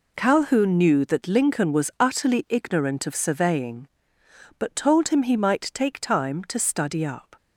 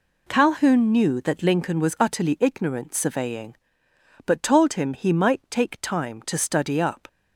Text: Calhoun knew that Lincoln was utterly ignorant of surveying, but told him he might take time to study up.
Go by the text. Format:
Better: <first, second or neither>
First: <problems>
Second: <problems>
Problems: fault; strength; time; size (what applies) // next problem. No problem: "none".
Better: first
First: none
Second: skips "of"; at 2.9 s